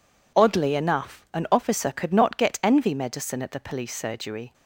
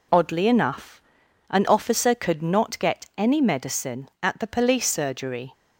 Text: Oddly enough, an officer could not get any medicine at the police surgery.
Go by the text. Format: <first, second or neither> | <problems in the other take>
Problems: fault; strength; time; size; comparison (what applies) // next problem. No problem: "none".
second | says "envy" for "any"; at 2.6 s